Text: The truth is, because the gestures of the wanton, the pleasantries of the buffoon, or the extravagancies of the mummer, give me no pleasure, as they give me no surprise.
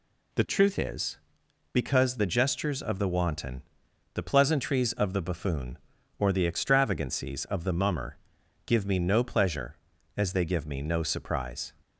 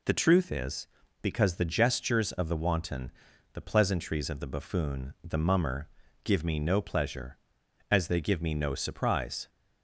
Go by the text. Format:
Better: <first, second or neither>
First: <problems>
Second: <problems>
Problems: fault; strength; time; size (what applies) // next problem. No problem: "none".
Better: first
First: none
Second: skips "or the extravagancies of"; at 5.1 s